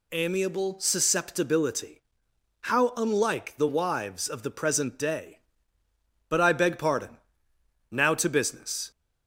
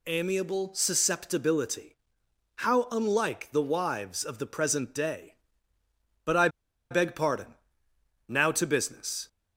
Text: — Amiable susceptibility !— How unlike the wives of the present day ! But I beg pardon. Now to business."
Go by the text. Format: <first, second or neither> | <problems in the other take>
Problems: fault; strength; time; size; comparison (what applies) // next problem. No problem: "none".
first | pauses between "I" and "beg"; at 6.4 s; 0.42 s long